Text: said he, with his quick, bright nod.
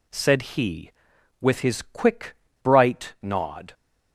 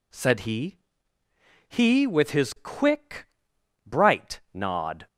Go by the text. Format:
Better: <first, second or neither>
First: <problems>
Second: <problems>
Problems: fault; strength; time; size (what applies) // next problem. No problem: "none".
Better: first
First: none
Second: says "he" twice; at 1.6 s